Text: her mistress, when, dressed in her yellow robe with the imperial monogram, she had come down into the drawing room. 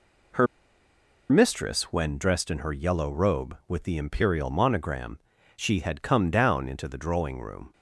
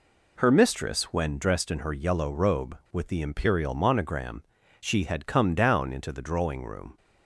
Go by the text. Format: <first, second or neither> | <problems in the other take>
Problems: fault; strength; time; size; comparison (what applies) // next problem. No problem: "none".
second | pauses between "her" and "mistress"; noticeable; at 0.4 s; 0.84 s long